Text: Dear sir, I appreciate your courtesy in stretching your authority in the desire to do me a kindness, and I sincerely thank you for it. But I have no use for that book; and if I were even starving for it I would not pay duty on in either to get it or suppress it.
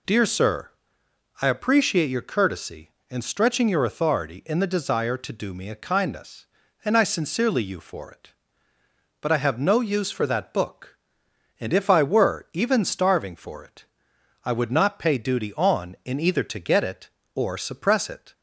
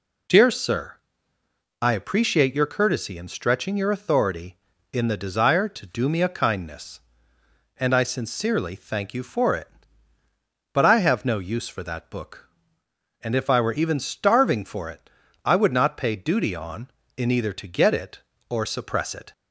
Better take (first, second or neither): second